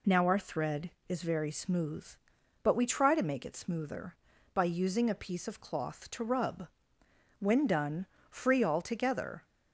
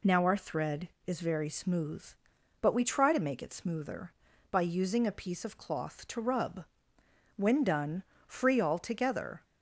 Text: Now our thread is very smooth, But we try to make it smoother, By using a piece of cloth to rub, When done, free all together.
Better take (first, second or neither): neither